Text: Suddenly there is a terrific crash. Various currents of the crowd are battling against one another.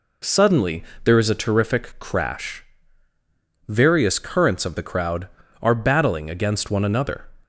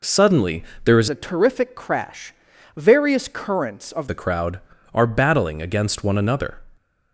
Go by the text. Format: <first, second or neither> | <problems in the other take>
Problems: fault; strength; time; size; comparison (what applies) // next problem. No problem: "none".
first | pauses between "Suddenly" and "there"; slight; at 0.6 s; 0.18 s long; slight in the first // changes voice from "a" to "of"; from 1.1 to 4.0 s; 2.9 s long